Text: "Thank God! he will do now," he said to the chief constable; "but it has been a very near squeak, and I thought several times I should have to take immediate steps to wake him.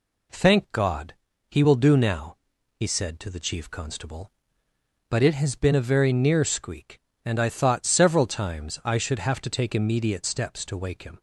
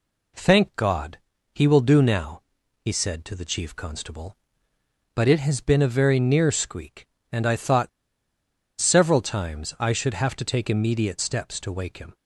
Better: first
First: none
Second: pauses between "thought" and "several"; noticeable; at 7.8 s; 0.90 s long

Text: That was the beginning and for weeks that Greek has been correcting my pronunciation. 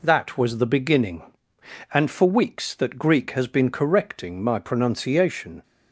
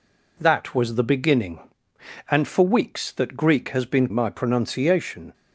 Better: first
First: none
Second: skips "correcting"; at 4.1 s

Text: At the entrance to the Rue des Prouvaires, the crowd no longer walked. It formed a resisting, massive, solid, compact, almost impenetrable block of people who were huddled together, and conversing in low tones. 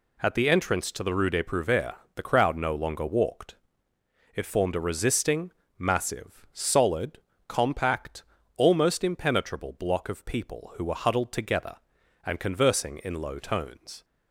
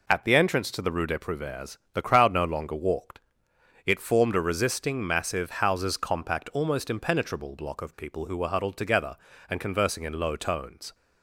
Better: first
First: none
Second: says "houses" for "solid"; at 5.4 s

